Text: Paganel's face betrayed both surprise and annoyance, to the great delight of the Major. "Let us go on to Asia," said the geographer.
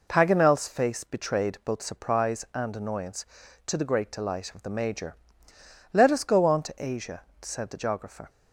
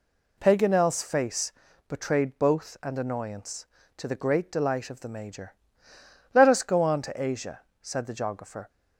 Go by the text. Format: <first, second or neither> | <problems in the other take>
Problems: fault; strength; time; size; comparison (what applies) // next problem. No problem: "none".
first | pauses between "face" and "betrayed"; slight; at 1.5 s; 0.36 s long // skips "surprise"; at 2.7 s